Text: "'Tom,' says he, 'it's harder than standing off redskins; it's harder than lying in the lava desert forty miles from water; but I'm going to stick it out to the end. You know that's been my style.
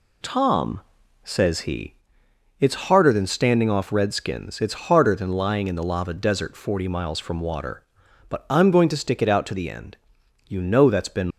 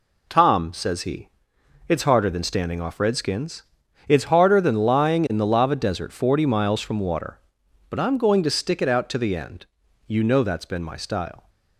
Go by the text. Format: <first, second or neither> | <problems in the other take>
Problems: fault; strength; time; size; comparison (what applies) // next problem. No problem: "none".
second | stops before "my style"; at 11.3 s